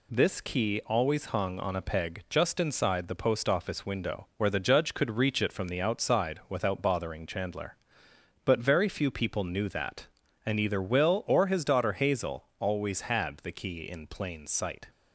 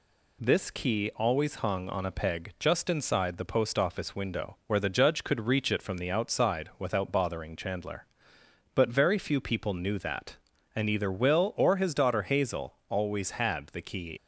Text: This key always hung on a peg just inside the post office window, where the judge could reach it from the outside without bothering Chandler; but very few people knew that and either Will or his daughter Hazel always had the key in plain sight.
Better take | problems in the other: first | stops before "in plain sight"; at 14.1 s

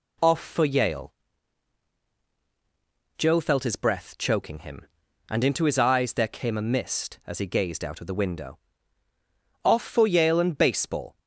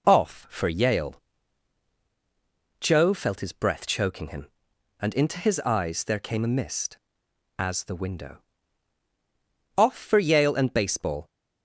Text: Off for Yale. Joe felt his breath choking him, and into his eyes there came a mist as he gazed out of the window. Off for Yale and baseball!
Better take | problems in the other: first | skips "he gazed out of"; at 7.8 s

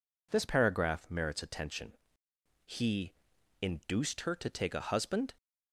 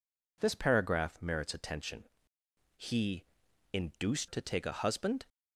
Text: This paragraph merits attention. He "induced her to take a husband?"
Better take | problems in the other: first | pauses between "He" and "induced"; noticeable; at 3.2 s; 0.48 s long; noticeable in the first // skips "her"; at 4.2 s

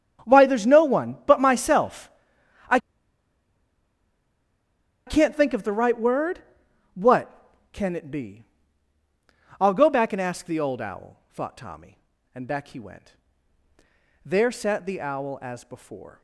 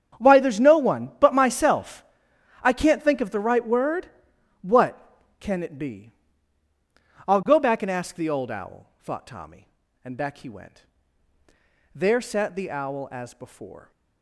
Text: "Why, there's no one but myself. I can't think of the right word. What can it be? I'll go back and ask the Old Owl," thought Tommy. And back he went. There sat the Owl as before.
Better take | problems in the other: second | starts louder than the rest; strong; until 1.3 s; 8.5 dB; strong in the second // pauses between "I" and "can't"; strong; at 2.7 s; 2.2 s long

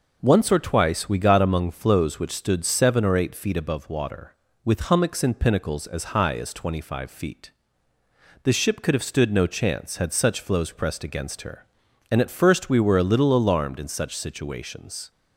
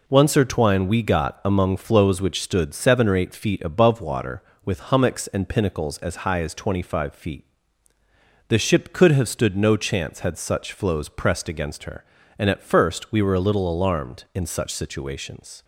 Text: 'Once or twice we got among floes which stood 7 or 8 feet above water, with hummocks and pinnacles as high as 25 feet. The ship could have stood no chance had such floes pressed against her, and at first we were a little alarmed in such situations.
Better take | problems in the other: first | says "twine" for "twice"; at 0.4 s

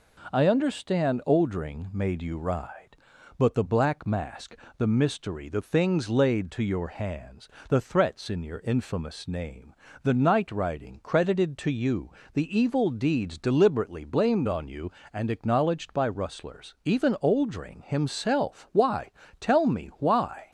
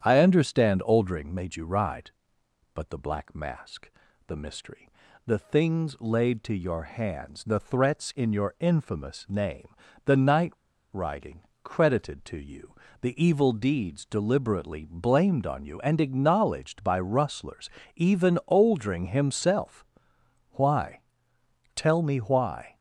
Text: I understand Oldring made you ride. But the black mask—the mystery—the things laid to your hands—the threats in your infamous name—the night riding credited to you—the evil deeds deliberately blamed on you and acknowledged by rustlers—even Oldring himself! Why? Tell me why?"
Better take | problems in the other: first | starts louder than the rest; strong; until 1.0 s; 8.5 dB // pauses between "night" and "riding"; at 10.5 s; 0.41 s long // pauses between "riding" and "credited"; slight; at 11.4 s; 0.24 s long

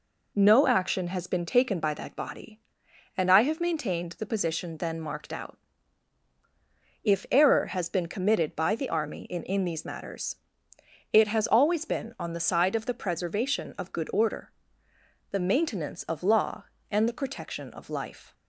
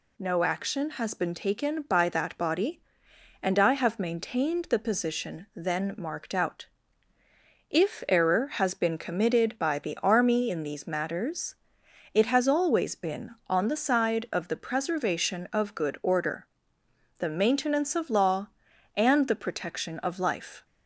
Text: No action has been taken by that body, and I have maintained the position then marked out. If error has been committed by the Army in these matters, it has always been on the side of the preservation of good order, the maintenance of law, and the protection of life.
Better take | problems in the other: second | says "in" twice; at 9.4 s

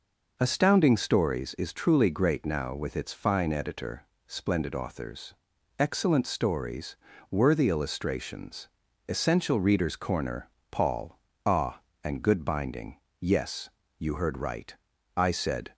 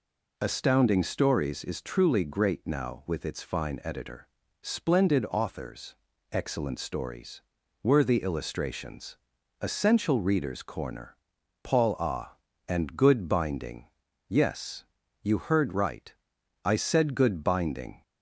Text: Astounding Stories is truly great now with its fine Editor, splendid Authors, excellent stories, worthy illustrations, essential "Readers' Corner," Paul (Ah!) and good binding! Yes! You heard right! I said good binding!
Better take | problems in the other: second | stops before "good binding"; at 15.7 s

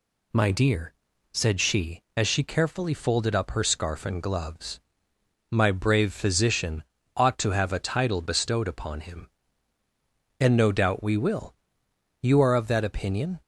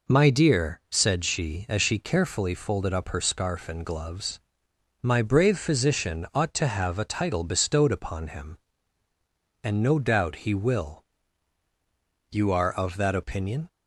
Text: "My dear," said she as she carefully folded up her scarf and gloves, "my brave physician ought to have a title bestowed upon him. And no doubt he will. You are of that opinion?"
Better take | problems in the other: second | pauses between "physician" and "ought"; slight; at 6.8 s; 0.32 s long // says "we" for "he"; at 11.0 s

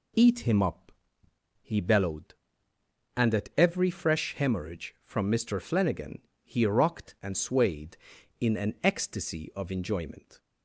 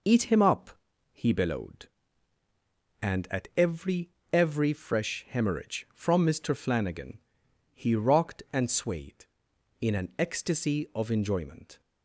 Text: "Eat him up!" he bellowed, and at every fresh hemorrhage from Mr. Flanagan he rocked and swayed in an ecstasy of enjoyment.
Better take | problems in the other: first | says "every" twice; at 4.3 s // pauses between "Flanagan" and "he"; noticeable; at 7.1 s; 0.56 s long; slight in the first

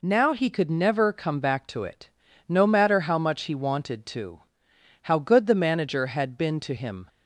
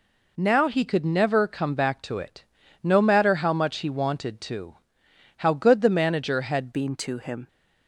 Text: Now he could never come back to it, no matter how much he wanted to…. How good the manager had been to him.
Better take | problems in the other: first | changes voice at "been"; from 6.7 s on; 0.7 s long

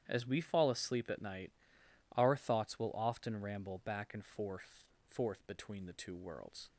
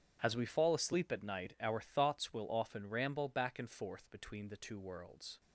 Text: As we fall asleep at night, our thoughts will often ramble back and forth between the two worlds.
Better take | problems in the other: second | starts louder than the rest; strong; until 1.0 s; 10 dB; strong in the second // says "forth" twice; at 5.0 s

